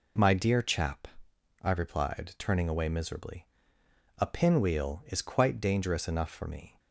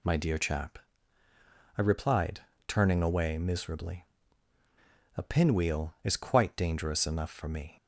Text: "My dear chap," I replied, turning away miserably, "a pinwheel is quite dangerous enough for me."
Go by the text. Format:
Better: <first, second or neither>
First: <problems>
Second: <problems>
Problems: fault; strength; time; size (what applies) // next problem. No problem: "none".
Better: neither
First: none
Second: none